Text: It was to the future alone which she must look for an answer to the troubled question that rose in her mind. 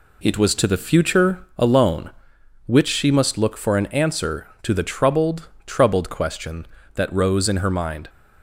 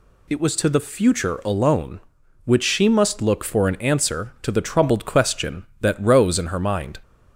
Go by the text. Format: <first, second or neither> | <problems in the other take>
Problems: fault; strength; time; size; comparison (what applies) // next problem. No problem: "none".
second | says "troubled" twice; at 5.6 s